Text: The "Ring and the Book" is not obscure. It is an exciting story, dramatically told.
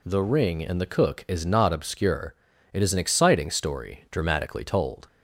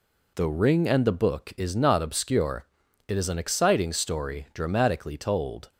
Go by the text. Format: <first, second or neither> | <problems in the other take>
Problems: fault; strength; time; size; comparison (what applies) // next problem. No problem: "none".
second | says "Cook" for "Book"; at 0.8 s